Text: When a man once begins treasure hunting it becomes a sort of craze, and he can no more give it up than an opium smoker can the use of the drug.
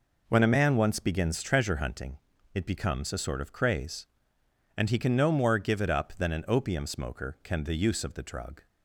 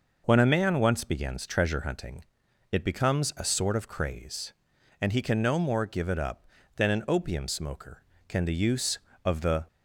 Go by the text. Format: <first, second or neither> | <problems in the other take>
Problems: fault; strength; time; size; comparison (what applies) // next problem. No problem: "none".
first | pauses between "hunting" and "it"; noticeable; at 2.2 s; 0.46 s long; slight in the first // stops before "drug"; at 9.6 s